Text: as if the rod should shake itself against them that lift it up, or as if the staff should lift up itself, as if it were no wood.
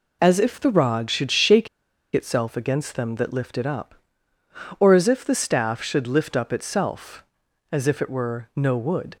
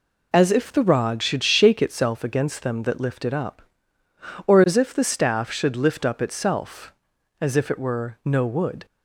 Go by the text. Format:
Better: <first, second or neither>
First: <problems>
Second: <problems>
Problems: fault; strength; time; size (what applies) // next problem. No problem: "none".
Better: second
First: pauses between "shake" and "itself"; noticeable; at 1.6 s; 0.46 s long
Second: none